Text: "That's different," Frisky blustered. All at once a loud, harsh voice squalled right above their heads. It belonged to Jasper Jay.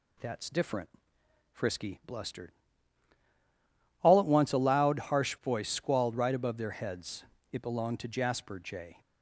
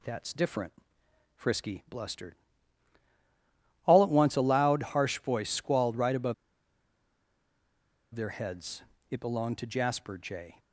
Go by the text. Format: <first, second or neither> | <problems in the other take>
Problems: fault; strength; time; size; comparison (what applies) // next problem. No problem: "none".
first | pauses between "above" and "their"; strong; at 6.3 s; 1.8 s long